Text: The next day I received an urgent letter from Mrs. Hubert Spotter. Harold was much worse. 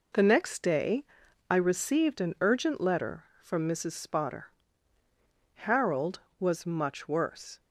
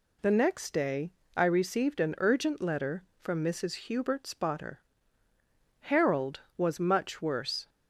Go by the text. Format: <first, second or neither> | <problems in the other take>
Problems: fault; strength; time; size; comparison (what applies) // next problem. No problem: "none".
second | pauses between "day" and "I"; at 1.0 s; 0.44 s long; slight in the second // skips "Hubert"; at 3.9 s